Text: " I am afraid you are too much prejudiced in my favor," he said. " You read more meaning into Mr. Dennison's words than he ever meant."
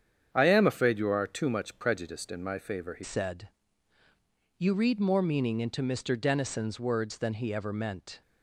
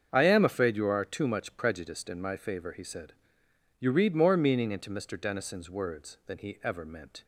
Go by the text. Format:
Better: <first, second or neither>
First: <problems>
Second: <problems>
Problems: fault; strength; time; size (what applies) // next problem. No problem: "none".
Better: second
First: starts louder than the rest; strong; until 1.3 s; 8.5 dB // changes voice at "said"; from 3.0 s on; 5.2 s long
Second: starts louder than the rest; strong; until 1.1 s; 7.5 dB